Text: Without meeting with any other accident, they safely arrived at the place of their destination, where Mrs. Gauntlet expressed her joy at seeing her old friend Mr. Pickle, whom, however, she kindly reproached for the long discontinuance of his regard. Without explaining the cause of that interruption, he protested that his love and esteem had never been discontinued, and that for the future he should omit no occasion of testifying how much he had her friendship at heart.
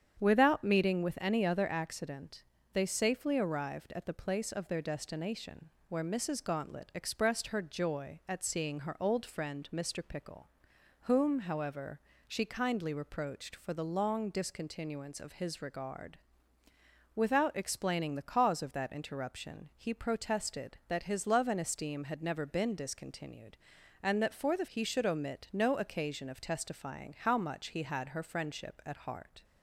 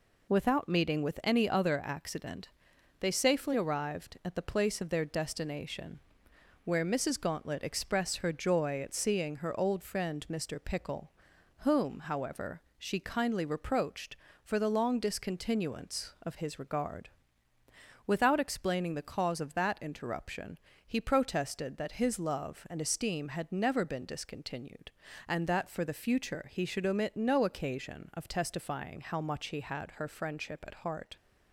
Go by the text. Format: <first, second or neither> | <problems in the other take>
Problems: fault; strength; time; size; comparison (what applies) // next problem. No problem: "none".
second | starts louder than the rest; strong; until 1.2 s; 8.5 dB // skips "future"; at 24.6 s